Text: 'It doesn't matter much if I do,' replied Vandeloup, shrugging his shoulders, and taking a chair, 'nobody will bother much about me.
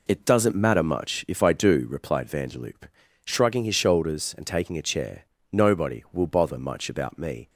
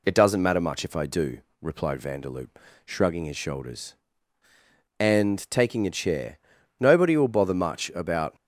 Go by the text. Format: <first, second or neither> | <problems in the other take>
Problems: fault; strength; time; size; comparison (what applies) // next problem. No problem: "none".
first | stops before "me"; at 8.3 s